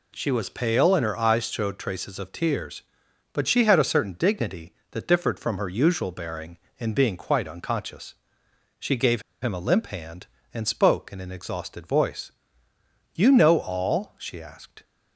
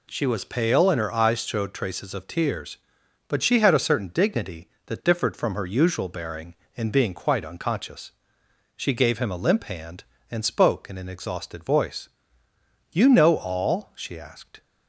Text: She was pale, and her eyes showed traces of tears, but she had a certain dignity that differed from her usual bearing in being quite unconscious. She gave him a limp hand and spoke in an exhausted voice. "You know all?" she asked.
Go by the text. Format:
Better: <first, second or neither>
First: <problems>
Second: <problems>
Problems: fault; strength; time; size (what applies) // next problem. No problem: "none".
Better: second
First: pauses between "gave" and "him"; slight; at 9.2 s; 0.20 s long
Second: none